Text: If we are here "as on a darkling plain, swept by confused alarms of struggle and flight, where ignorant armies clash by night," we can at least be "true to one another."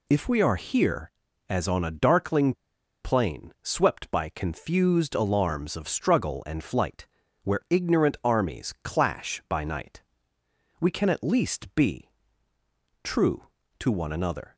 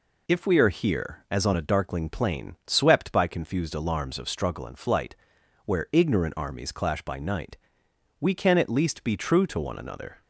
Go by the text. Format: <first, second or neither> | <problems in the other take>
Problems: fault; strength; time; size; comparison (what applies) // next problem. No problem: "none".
second | pauses between "darkling" and "plain"; noticeable; at 2.5 s; 0.50 s long // pauses between "be" and "true"; noticeable; at 12.0 s; 0.94 s long